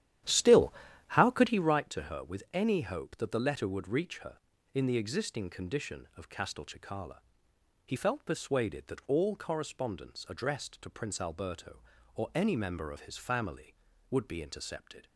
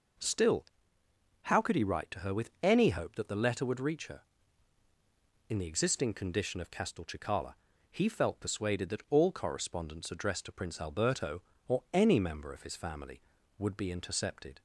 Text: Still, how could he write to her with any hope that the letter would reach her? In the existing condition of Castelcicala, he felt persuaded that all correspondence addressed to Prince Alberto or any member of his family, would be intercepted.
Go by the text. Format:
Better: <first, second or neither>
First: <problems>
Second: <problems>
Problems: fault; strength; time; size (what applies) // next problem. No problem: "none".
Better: second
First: starts louder than the rest; strong; until 1.8 s; 11.5 dB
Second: none